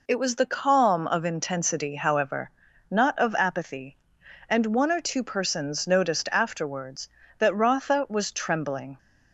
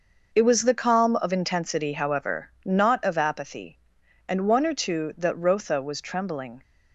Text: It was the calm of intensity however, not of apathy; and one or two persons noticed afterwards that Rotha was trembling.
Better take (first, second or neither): first